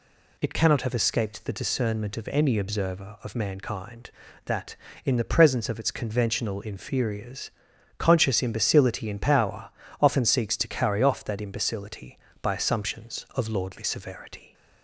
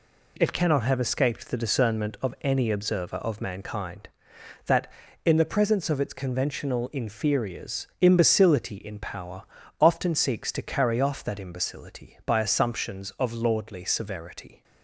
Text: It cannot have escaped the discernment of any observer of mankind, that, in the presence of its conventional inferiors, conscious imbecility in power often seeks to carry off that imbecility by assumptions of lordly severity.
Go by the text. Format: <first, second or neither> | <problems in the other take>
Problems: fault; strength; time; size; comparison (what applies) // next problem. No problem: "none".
first | skips "conscious"; at 7.9 s // pauses between "power" and "often"; slight; at 9.4 s; 0.36 s long; slight in the first